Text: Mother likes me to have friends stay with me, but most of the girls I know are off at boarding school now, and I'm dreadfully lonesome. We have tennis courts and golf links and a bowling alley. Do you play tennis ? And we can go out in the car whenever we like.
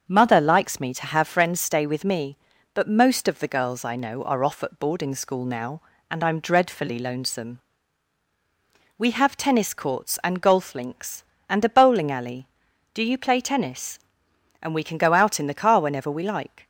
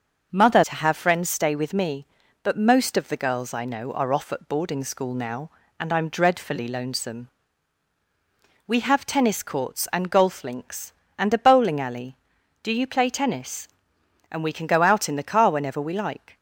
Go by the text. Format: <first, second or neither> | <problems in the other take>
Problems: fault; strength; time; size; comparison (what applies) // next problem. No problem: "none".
first | starts louder than the rest; noticeable; until 1.3 s; 6 dB; also in the first // skips "likes me"; at 0.6 s